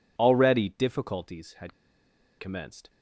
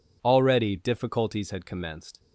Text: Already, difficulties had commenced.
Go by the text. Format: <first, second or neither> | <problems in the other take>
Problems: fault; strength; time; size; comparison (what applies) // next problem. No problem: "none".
second | pauses between "had" and "commenced"; noticeable; at 1.7 s; 0.66 s long